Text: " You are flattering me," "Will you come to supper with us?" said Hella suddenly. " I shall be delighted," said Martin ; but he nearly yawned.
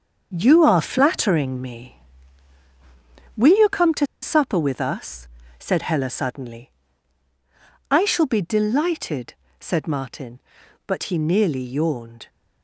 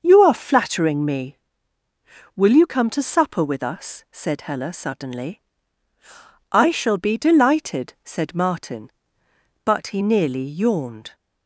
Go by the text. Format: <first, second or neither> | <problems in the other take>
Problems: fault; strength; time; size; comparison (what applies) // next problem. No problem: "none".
second | starts louder than the rest; until 1.3 s; 7 dB; also in the second // pauses between "to" and "supper"; slight; at 4.0 s; 0.16 s long